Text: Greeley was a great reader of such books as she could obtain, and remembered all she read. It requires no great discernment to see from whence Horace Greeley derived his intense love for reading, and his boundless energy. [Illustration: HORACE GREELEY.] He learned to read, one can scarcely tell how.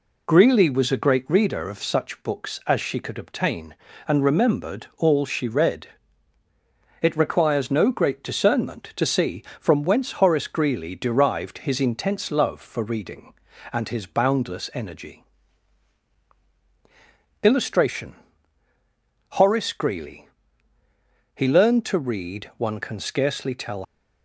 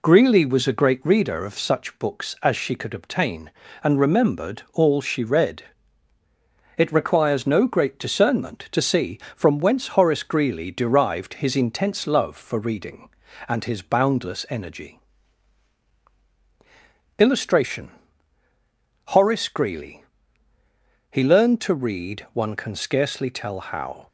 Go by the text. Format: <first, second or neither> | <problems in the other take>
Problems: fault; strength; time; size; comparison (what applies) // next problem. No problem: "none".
second | stops before "how"; at 23.8 s